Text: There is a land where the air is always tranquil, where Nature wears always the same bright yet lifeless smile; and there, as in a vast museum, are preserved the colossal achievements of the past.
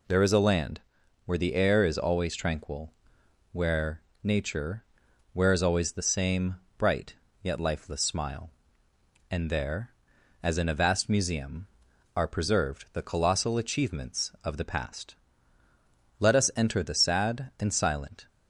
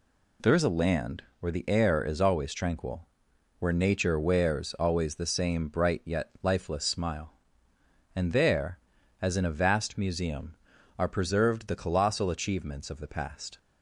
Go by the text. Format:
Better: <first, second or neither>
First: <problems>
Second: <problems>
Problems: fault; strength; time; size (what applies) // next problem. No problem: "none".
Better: second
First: pauses between "land" and "where"; at 0.8 s; 0.44 s long // pauses between "where" and "Nature"; slight; at 4.0 s; 0.22 s long // pauses between "Nature" and "wears"; noticeable; at 4.8 s; 0.52 s long // pauses between "same" and "bright"; slight; at 6.5 s; 0.23 s long // pauses between "bright" and "yet"; slight; at 7.1 s; 0.28 s long // goes on to say "Let us enter the sad and silent"; strong; from 16.1 s on; 2.0 s long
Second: pauses between "land" and "where"; slight; at 1.2 s; 0.18 s long